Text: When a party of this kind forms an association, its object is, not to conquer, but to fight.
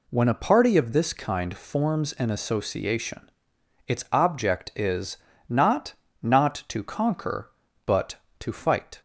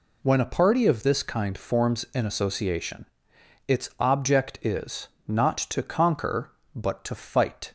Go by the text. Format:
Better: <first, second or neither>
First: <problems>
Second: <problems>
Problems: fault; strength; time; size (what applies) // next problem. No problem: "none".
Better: second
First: says "not" twice; at 6.2 s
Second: none